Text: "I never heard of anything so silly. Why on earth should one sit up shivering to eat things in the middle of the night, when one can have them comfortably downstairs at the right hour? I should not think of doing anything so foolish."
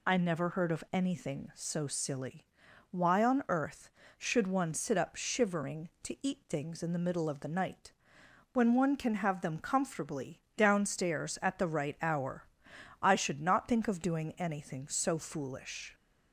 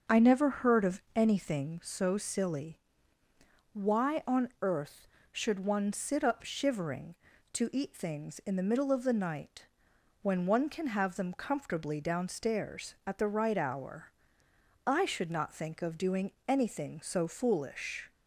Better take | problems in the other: first | starts louder than the rest; until 1.8 s; 6.5 dB // pauses between "doing" and "anything"; slight; at 16.3 s; 0.16 s long

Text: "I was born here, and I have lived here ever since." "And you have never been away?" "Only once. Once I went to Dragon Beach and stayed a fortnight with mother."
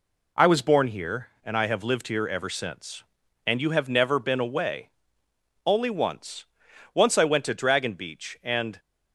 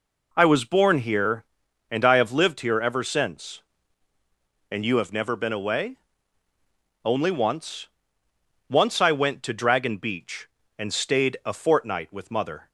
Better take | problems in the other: second | stops before "stayed a fortnight with mother"; at 8.7 s

